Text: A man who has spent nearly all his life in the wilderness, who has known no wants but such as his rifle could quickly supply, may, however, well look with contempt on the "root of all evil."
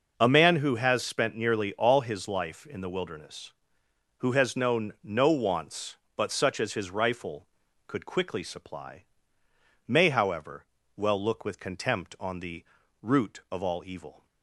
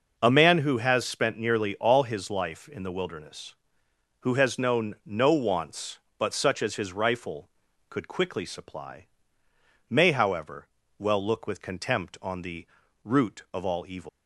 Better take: first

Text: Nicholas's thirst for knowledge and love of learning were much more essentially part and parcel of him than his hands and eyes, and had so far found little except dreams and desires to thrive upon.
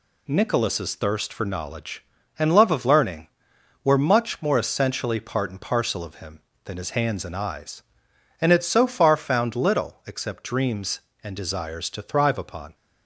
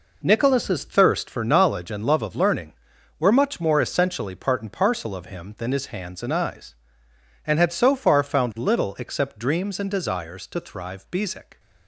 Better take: first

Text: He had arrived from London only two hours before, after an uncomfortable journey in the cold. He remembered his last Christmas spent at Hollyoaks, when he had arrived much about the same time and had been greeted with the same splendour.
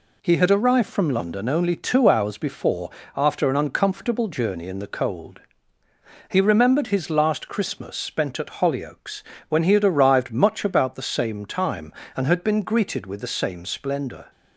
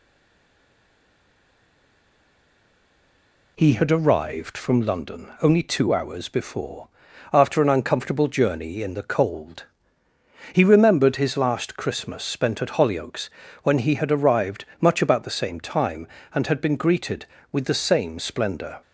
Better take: first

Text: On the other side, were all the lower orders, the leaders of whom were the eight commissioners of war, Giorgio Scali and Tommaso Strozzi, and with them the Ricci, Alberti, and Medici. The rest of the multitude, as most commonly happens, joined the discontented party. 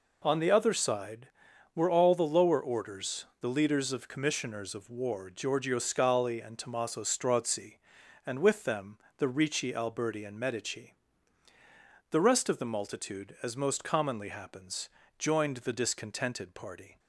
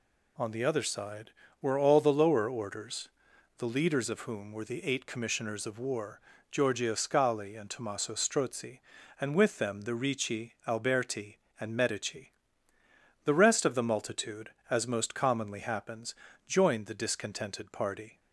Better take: second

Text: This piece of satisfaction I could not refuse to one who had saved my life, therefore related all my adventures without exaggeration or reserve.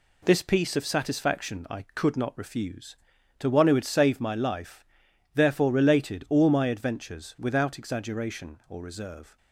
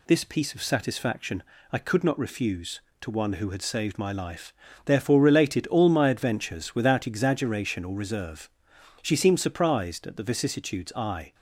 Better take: first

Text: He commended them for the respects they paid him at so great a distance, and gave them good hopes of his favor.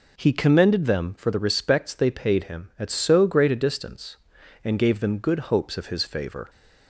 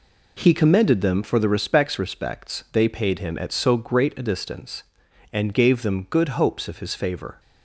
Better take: first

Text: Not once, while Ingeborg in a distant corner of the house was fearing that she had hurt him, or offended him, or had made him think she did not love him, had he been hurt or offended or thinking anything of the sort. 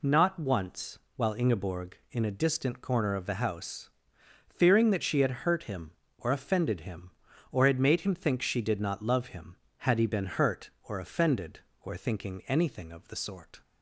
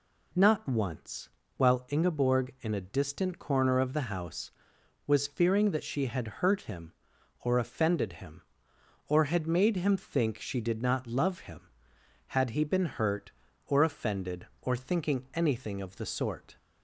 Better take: second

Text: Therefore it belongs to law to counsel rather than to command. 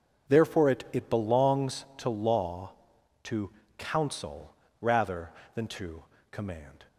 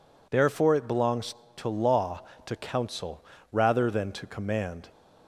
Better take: second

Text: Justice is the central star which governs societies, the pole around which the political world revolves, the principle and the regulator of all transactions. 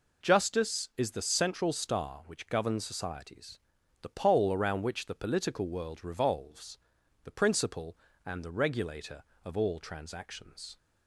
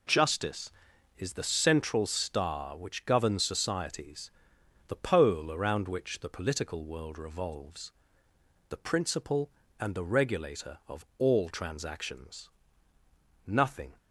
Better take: first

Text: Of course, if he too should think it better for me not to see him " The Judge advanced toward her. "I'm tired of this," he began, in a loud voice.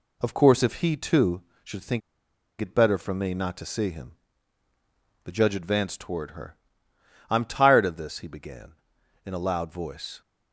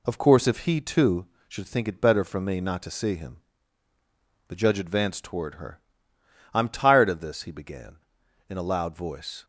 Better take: second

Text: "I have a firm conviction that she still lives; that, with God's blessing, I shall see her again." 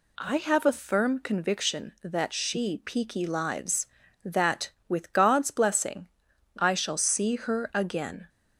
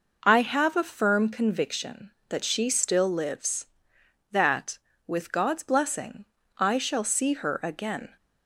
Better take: second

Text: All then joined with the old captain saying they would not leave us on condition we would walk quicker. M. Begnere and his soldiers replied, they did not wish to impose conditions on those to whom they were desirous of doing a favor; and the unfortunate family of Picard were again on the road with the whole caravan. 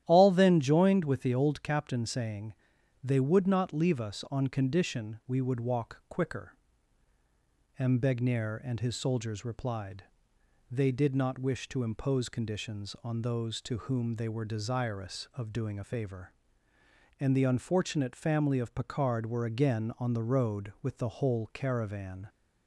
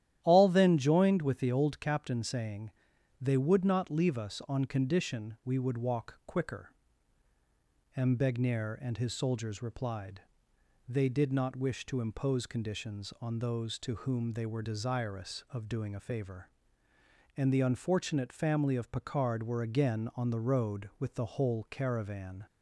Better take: neither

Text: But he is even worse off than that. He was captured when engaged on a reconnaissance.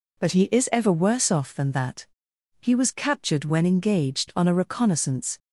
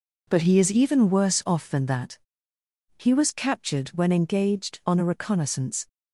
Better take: second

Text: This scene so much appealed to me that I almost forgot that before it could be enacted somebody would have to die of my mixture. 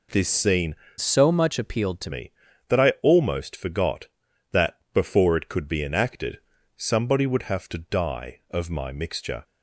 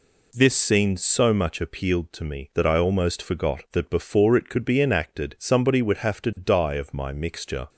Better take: second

